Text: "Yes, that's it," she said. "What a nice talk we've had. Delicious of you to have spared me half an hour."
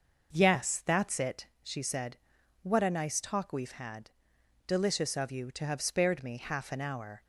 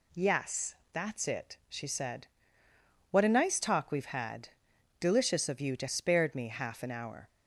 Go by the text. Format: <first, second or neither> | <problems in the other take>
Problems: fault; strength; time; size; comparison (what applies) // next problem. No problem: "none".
first | skips "have"; at 5.8 s